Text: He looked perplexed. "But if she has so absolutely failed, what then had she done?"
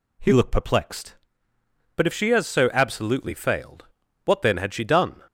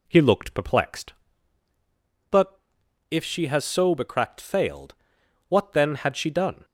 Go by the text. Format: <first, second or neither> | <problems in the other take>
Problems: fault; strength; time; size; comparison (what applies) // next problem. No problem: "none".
first | pauses between "But" and "if"; noticeable; at 2.5 s; 0.52 s long // says "becracked" for "absolutely"; at 3.9 s